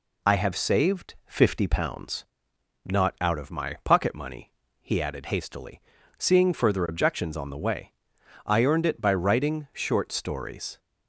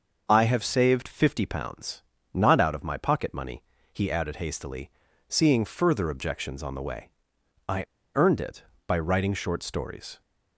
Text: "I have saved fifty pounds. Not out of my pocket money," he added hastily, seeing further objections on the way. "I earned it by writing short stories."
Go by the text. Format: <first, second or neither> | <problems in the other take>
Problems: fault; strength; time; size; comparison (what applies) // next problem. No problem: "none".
first | starts louder than the rest; until 1.2 s; 6 dB // pauses between "I" and "earned"; slight; at 7.8 s; 0.29 s long